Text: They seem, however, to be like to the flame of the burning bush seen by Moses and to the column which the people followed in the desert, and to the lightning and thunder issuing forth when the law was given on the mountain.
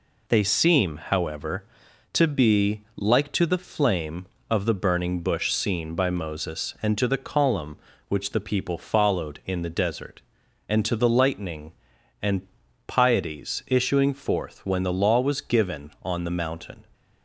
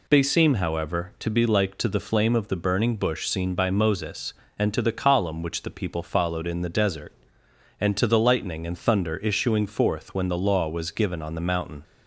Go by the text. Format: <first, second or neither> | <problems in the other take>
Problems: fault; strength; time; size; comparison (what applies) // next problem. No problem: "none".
second | says "pieties" for "thunder"; at 12.8 s